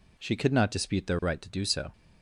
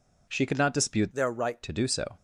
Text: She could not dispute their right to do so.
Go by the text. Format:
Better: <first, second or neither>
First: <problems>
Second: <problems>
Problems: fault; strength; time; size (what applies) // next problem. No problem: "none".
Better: first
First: none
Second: changes voice from "their" to "right"; from 1.1 to 1.6 s; 0.5 s long